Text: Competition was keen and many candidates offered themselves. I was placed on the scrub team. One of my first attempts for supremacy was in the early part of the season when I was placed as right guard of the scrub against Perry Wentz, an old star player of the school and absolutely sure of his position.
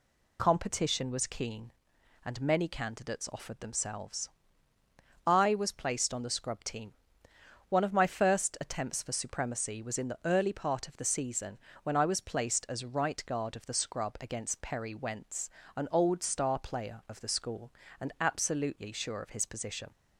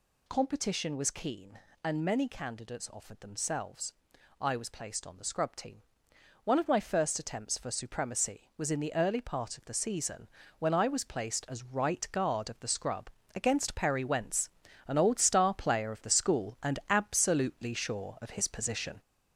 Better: first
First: pauses between "season" and "when"; slight; at 11.5 s; 0.24 s long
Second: gets louder; noticeable; throughout; 5 dB // pauses between "season" and "when"; slight; at 10.2 s; 0.30 s long // pauses between "scrub" and "against"; slight; at 13.0 s; 0.26 s long

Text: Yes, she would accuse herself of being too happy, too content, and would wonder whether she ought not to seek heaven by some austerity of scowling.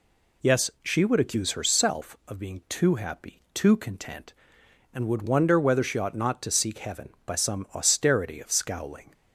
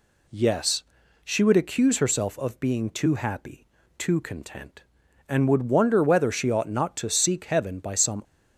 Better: first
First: none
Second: stops before "austerity of scowling"; at 8.2 s

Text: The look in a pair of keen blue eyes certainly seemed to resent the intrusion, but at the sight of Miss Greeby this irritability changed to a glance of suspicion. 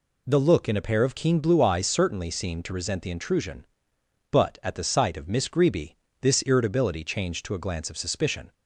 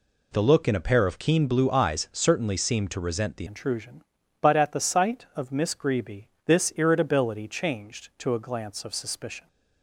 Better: first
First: pauses between "Greeby" and "this"; slight; at 5.9 s; 0.24 s long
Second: changes voice at "intrusion"; from 3.4 s on; 6.0 s long // pauses between "Greeby" and "this"; slight; at 6.2 s; 0.16 s long

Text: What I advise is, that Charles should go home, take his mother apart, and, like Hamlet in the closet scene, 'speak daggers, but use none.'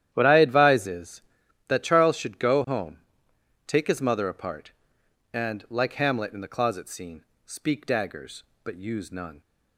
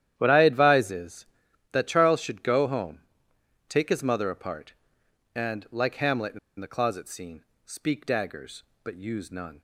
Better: first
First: starts louder than the rest; strong; until 1.1 s; 11 dB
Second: starts louder than the rest; strong; until 1.1 s; 11 dB // pauses between "in" and "the"; slight; at 6.3 s; 0.21 s long

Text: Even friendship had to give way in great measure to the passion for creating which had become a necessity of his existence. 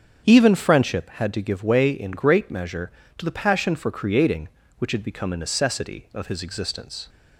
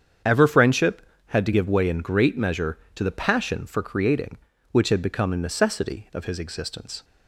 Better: first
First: starts louder than the rest; strong; until 1.2 s; 7.5 dB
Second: starts louder than the rest; strong; until 1.5 s; 8 dB // says "Ever" for "Even"; at 0.2 s

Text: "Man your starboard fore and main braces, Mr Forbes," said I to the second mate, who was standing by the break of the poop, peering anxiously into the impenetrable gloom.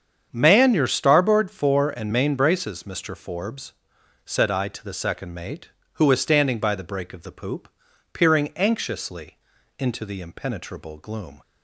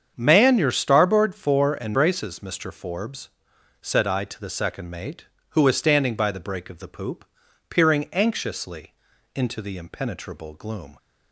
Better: first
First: starts louder than the rest; strong; until 1.3 s; 7.5 dB // pauses between "anxiously" and "into"; at 9.3 s; 0.40 s long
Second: starts louder than the rest; strong; until 1.1 s; 7.5 dB // skips "main"; at 1.9 s // pauses between "anxiously" and "into"; at 8.9 s; 0.40 s long

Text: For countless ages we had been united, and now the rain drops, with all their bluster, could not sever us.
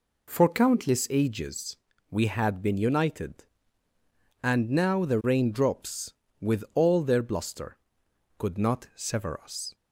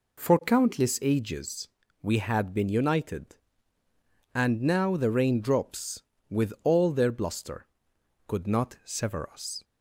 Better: neither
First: pauses between "ages" and "we"; slight; at 1.7 s; 0.36 s long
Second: pauses between "ages" and "we"; slight; at 1.6 s; 0.36 s long

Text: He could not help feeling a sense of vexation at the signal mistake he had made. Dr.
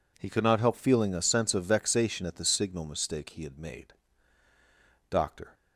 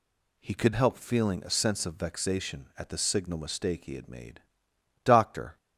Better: first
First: none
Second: skips "not"; at 0.7 s

